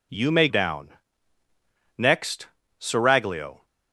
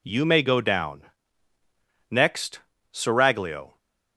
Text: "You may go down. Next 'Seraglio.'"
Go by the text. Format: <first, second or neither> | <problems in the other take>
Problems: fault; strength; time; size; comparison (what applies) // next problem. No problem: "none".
second | skips "go"; at 0.4 s // pauses between "Next" and "Seraglio"; slight; at 2.4 s; 0.32 s long; slight in the second